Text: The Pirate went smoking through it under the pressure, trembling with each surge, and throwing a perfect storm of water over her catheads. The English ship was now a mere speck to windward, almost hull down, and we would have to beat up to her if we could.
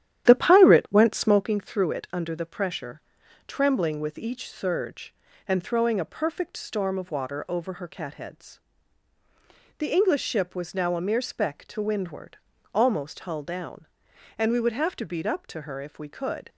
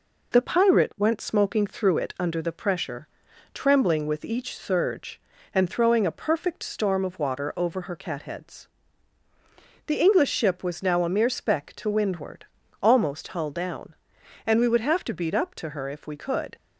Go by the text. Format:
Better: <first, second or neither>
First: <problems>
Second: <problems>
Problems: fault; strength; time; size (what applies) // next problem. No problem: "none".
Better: second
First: starts louder than the rest; strong; until 1.5 s; 11 dB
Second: none